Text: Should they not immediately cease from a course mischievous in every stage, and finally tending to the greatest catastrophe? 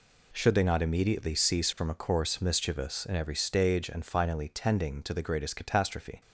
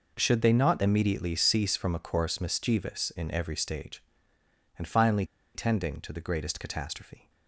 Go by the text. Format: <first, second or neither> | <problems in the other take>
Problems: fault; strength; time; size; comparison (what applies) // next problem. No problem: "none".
first | pauses between "finally" and "tending"; slight; at 5.2 s; 0.29 s long